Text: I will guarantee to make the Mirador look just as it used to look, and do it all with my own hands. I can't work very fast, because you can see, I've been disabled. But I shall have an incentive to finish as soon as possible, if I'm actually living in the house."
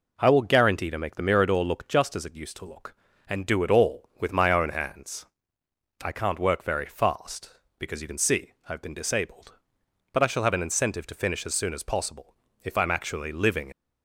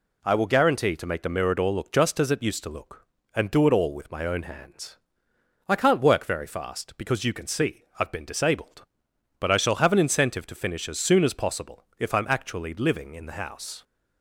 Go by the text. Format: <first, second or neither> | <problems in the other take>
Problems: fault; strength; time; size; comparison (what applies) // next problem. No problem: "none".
second | stops before "in the house"; at 13.7 s